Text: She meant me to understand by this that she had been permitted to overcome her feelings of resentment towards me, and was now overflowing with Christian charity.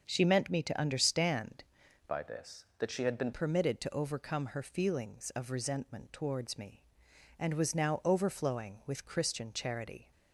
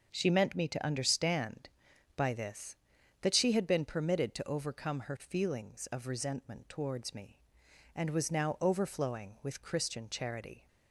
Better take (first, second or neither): second